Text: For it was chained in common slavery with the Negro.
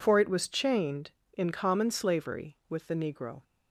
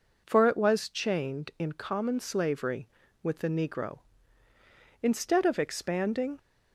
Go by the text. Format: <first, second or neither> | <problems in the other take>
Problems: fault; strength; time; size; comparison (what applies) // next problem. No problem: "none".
first | goes on to say "Instead of expanding"; from 5.0 s on; 1.3 s long